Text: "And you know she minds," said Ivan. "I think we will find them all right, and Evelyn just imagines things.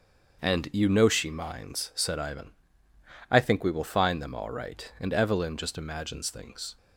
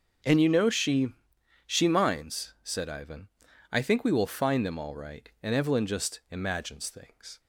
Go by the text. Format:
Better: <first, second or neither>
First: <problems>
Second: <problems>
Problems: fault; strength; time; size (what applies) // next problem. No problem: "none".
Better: first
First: starts louder than the rest; until 1.4 s; 6.5 dB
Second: starts louder than the rest; until 1.8 s; 6.5 dB // says "she" twice; at 1.6 s